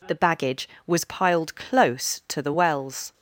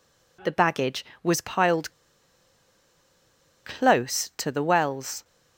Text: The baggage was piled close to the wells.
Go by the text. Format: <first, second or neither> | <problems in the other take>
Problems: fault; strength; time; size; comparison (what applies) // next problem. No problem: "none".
first | pauses between "piled" and "close"; strong; at 1.9 s; 1.7 s long